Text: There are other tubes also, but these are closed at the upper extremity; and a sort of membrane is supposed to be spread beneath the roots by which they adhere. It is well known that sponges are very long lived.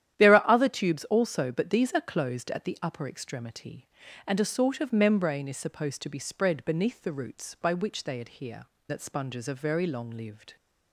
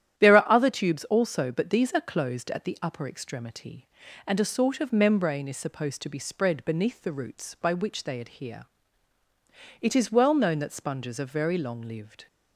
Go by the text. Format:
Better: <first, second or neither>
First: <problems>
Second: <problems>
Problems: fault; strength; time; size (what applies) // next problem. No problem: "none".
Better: second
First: starts louder than the rest; strong; until 1.1 s; 11 dB // skips "It is well known"; at 8.7 s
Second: starts louder than the rest; strong; until 1.2 s; 11 dB